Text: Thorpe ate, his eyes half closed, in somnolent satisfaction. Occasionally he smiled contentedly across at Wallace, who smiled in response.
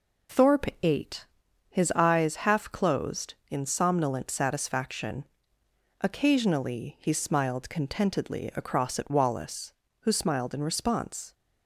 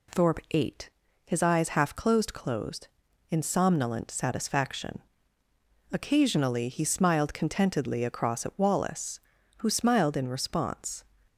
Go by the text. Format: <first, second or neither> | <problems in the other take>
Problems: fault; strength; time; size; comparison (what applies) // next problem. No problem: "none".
first | says "closed" twice; at 2.3 s